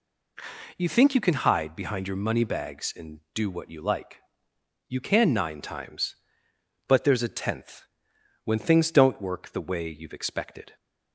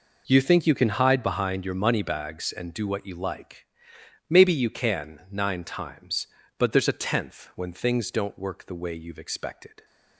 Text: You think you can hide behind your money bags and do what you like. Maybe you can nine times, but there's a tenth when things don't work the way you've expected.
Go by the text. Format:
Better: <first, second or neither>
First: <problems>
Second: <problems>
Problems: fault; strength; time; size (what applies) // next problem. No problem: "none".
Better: second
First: skips "Maybe"; at 4.5 s // pauses between "tenth" and "when"; noticeable; at 7.8 s; 0.58 s long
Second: none